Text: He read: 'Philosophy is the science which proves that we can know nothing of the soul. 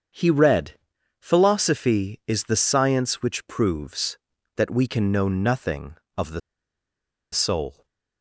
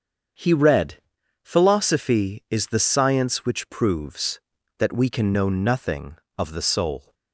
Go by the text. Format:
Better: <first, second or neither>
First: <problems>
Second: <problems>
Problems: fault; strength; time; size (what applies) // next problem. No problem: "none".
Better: second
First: starts louder than the rest; strong; until 1.5 s; 7 dB // pauses between "the" and "soul"; noticeable; at 6.4 s; 0.92 s long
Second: starts louder than the rest; strong; until 1.8 s; 7 dB